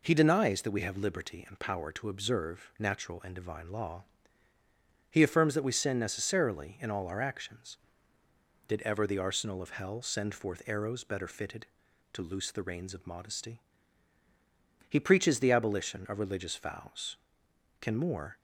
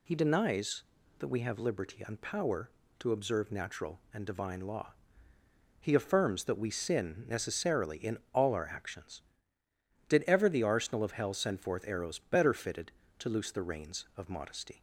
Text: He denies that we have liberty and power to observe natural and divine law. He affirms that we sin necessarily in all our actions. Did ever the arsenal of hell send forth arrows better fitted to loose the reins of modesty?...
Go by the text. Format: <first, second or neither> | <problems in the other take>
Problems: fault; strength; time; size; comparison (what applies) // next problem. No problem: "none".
second | goes on to say "He preaches the abolition of religious vows Can more"; strong; from 14.8 s on; 3.4 s long